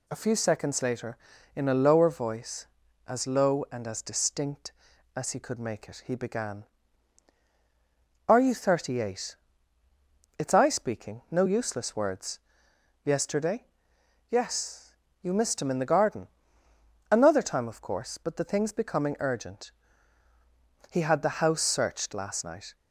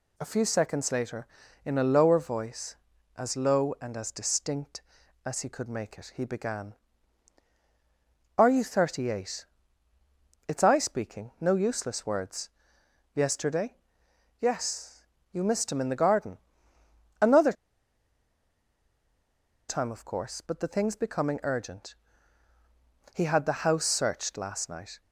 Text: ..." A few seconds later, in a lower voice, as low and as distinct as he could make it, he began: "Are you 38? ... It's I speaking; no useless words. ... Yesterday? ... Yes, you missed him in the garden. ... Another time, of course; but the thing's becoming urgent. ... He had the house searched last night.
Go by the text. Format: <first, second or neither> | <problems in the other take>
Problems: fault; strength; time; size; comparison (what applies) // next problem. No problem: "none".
first | pauses between "Another" and "time"; strong; at 17.5 s; 2.1 s long